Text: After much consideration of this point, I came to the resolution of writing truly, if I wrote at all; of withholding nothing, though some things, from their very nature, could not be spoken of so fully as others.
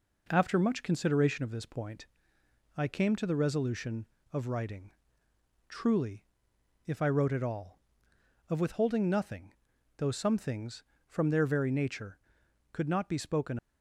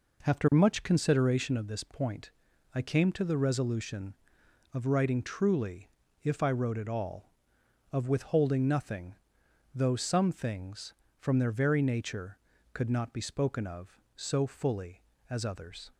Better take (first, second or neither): second